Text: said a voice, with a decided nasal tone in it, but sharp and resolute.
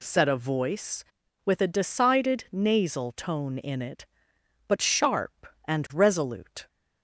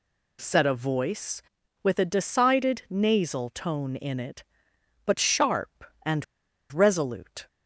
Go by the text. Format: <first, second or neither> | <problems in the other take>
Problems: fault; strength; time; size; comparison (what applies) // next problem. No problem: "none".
first | pauses between "and" and "resolute"; noticeable; at 6.2 s; 0.48 s long